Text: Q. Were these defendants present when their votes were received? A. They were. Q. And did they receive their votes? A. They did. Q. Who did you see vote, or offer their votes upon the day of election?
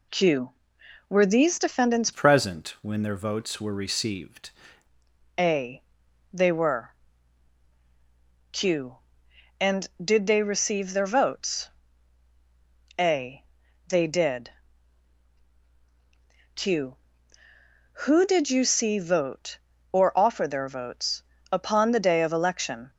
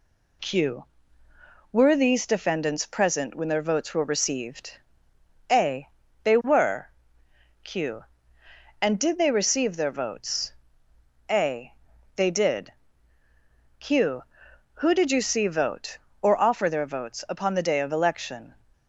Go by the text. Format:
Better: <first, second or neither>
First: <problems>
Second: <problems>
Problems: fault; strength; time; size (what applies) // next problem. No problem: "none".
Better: second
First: changes voice from "present" to "received"; from 2.1 to 4.4 s; 2.3 s long // pauses between "votes" and "upon"; slight; at 21.2 s; 0.30 s long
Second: none